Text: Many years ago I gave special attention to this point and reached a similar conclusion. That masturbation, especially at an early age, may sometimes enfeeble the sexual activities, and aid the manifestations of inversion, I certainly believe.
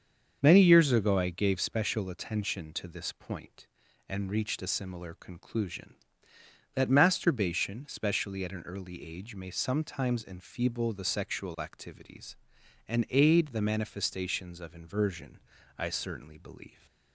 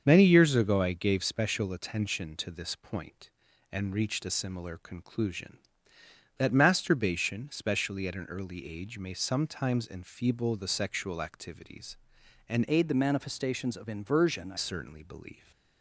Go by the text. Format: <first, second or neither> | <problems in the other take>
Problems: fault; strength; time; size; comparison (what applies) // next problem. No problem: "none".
first | starts louder than the rest; until 1.0 s; 7 dB; also in the first // changes voice from "aid" to "I"; from 12.6 to 14.5 s; 1.9 s long